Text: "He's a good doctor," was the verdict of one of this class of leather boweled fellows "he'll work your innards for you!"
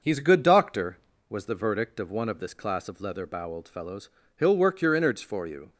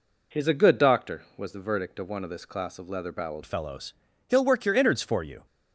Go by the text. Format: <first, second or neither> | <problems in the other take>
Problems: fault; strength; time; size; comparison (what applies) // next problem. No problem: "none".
first | changes voice at "fellows"; from 3.4 s on; 2.0 s long // pauses between "fellows" and "he'll"; slight; at 3.9 s; 0.34 s long; slight in the first